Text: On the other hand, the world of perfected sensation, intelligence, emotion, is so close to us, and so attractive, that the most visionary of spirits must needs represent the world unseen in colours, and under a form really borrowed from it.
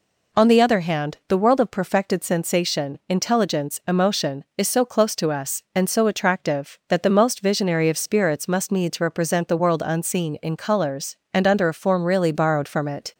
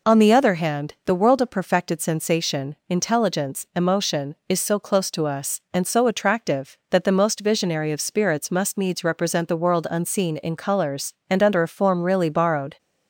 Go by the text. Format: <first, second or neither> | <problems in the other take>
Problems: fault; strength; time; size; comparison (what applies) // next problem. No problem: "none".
first | stops before "from it"; at 12.7 s